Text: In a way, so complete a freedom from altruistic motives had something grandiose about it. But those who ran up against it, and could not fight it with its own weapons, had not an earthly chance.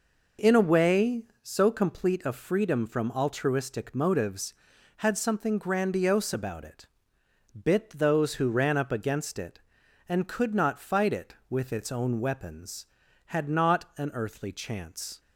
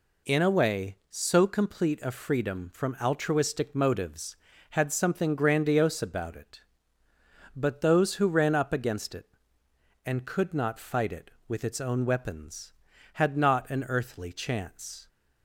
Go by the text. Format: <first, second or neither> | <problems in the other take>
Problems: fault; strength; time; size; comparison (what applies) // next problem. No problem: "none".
second | says "Bit" for "But"; at 7.6 s